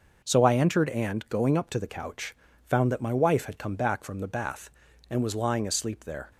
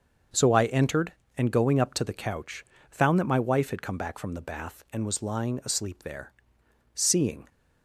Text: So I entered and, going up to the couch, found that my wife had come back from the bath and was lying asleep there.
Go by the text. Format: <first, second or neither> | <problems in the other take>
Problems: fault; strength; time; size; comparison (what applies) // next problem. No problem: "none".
first | starts louder than the rest; until 1.5 s; 6.5 dB; noticeable in the first // goes on to say "Seeing"; from 6.9 s on; 0.54 s long